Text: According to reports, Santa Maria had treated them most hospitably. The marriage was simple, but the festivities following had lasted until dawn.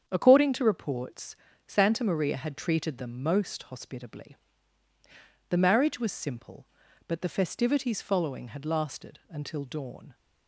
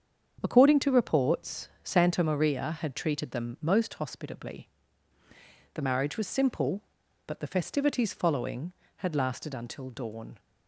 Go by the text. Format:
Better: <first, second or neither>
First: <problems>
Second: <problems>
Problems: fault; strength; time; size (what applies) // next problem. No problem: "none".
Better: neither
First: starts louder than the rest; strong; until 1.0 s; 8 dB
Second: starts louder than the rest; strong; until 1.4 s; 7.5 dB